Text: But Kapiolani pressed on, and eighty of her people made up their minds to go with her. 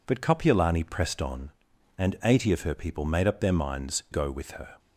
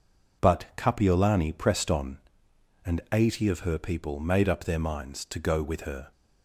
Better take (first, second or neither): second